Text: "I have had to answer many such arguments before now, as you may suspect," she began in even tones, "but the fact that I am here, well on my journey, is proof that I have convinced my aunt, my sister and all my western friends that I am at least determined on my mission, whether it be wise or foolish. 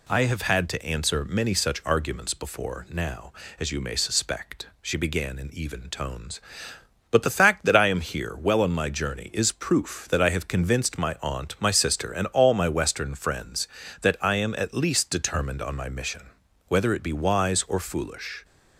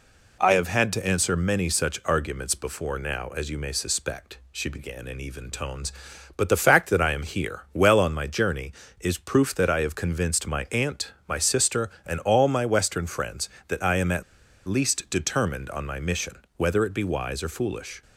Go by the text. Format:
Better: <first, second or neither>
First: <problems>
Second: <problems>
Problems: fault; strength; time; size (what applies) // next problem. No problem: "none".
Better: first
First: none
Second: pauses between "at" and "least"; at 14.2 s; 0.44 s long